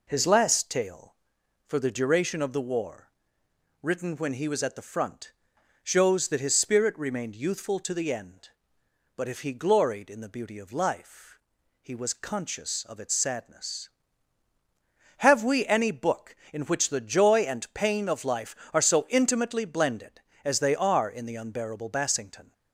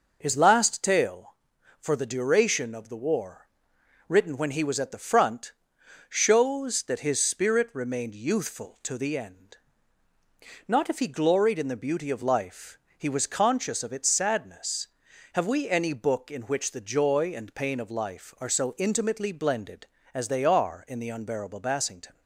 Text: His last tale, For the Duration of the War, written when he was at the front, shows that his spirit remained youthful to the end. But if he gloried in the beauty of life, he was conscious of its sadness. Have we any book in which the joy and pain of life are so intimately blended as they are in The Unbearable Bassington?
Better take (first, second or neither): first